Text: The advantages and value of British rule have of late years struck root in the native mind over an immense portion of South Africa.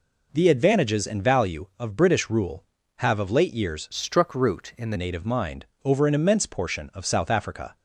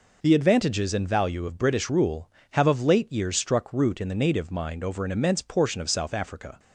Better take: second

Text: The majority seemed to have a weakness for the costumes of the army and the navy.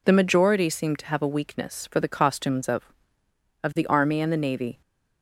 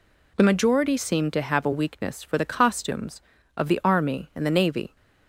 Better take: second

